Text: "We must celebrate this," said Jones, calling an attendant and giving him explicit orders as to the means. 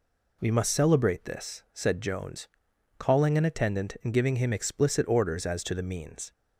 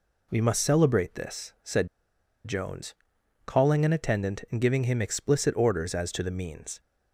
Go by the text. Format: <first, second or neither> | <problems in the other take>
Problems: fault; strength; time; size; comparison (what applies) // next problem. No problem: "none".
first | pauses between "said" and "Jones"; noticeable; at 1.8 s; 0.58 s long